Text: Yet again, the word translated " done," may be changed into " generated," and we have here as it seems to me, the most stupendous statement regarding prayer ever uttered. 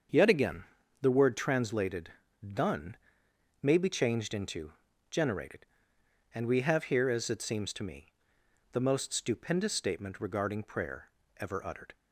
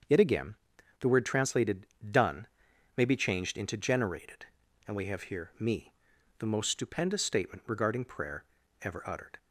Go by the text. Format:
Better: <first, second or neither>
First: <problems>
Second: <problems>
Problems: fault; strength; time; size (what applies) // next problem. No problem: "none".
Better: first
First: starts louder than the rest; until 1.4 s; 7 dB // pauses between "prayer" and "ever"; slight; at 11.1 s; 0.26 s long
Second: starts louder than the rest; until 1.5 s; 7 dB // skips "as it seems to"; at 5.5 s // pauses between "prayer" and "ever"; at 8.4 s; 0.38 s long